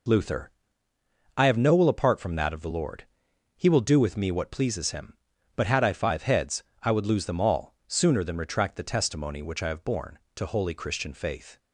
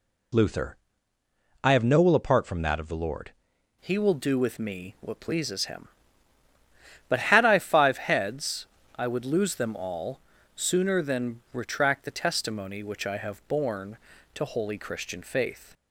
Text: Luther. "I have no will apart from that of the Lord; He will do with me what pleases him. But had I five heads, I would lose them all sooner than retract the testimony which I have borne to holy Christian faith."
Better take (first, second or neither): first